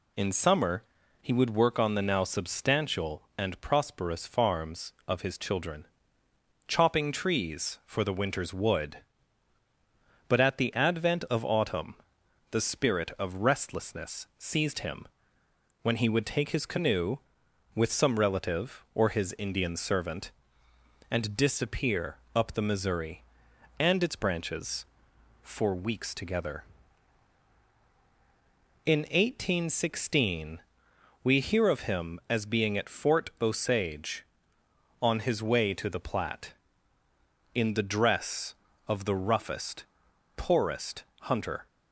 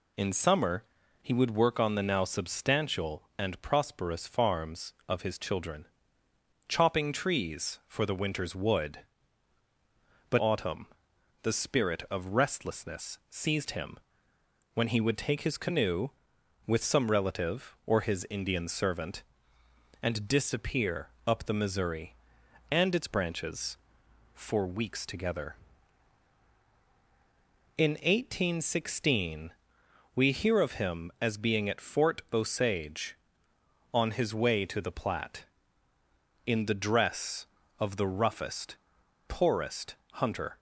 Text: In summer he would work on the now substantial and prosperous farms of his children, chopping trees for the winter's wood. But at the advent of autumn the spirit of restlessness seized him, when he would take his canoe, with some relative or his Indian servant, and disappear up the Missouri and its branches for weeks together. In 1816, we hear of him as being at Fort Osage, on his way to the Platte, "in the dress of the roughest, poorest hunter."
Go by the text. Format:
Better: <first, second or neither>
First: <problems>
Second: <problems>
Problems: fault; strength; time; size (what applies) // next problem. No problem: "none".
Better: first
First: pauses between "summer" and "he"; at 0.8 s; 0.40 s long // pauses between "autumn" and "the"; noticeable; at 11.9 s; 0.56 s long // pauses between "disappear" and "up"; slight; at 22.1 s; 0.18 s long // pauses between "poorest" and "hunter"; slight; at 41.0 s; 0.18 s long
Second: pauses between "summer" and "he"; at 0.8 s; 0.40 s long // skips "at the advent of"; at 10.3 s // pauses between "autumn" and "the"; noticeable; at 10.8 s; 0.56 s long // pauses between "disappear" and "up"; slight; at 21.0 s; 0.18 s long // pauses between "poorest" and "hunter"; slight; at 39.9 s; 0.18 s long